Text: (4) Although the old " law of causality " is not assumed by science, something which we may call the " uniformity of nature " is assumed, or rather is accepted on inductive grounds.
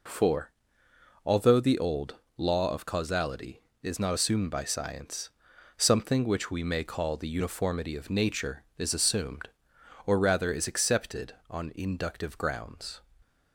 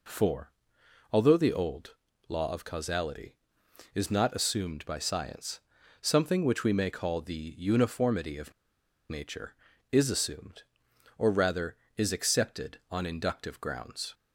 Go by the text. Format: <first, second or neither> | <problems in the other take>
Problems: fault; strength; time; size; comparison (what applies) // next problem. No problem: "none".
first | pauses between "of" and "nature"; noticeable; at 8.5 s; 0.57 s long